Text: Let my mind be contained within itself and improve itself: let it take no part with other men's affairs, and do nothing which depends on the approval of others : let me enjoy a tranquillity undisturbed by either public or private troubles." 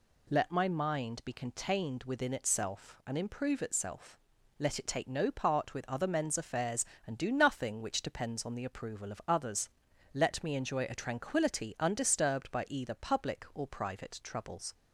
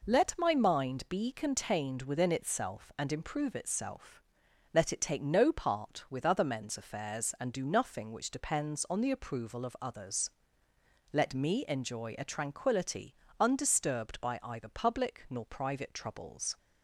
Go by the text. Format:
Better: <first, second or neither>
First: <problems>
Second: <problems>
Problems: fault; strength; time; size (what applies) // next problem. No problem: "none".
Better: first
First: none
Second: pauses between "tranquillity" and "undisturbed"; slight; at 13.1 s; 0.24 s long // says "nor" for "or"; at 15.2 s